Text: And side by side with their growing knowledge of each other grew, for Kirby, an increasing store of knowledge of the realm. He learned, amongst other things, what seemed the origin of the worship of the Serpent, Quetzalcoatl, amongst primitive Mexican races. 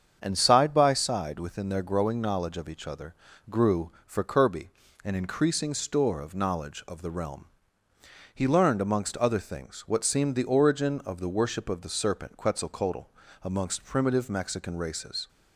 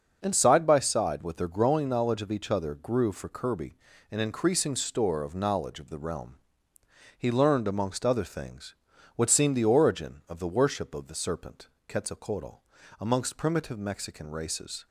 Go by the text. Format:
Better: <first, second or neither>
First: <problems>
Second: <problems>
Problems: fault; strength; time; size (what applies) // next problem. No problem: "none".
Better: second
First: starts louder than the rest; strong; until 1.2 s; 7.5 dB // says "within" for "with"; at 1.3 s // pauses between "other" and "grew"; slight; at 3.1 s; 0.36 s long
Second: starts louder than the rest; until 1.2 s; 6.5 dB